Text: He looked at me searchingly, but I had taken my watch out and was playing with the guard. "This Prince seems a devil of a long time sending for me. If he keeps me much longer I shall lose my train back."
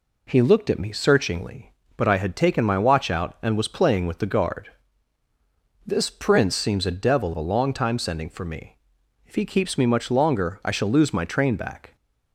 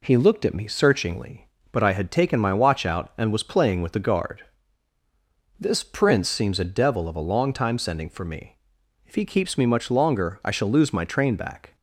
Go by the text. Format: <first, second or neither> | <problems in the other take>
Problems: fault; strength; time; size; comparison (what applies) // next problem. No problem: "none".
second | skips "of"; at 7.3 s